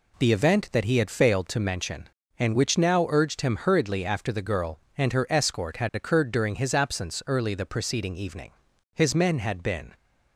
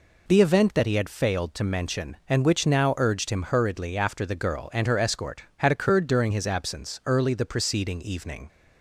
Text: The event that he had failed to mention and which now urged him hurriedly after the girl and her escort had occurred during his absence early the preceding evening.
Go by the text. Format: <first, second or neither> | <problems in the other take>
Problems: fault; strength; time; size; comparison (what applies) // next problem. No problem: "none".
second | goes on to say "His men had been"; noticeable; from 8.9 s on; 0.98 s long